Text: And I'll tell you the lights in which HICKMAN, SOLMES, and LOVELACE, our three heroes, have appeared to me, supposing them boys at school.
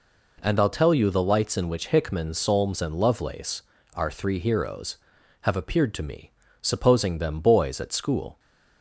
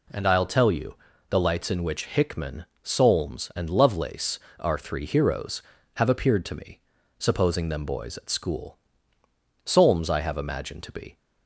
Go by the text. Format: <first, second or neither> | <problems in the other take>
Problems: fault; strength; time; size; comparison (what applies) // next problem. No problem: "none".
first | pauses between "you" and "the"; slight; at 0.9 s; 0.34 s long // goes on to say "Solmes I have imagined to be"; from 9.6 s on; 1.5 s long